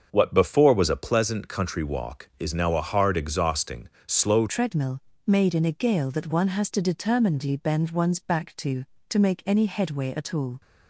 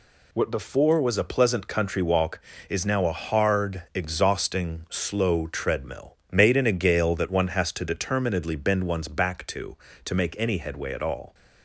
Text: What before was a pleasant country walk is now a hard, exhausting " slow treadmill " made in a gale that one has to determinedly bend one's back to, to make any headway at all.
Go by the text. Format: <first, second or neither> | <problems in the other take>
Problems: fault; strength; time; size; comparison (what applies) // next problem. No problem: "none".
second | starts louder than the rest; until 1.1 s; 6.5 dB // changes voice at "treadmill"; from 4.4 s on; 6.2 s long